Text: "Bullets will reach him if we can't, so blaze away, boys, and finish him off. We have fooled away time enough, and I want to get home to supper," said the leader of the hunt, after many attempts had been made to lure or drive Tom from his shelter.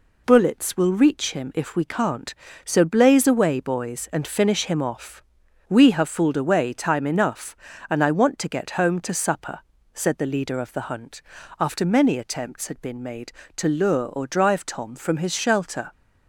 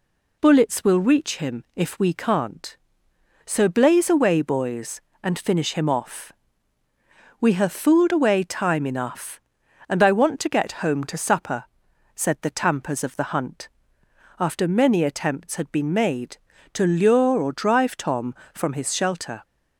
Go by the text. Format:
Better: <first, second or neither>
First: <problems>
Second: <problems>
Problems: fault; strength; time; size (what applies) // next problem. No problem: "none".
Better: first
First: none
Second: says "tampers" for "leader"; at 12.5 s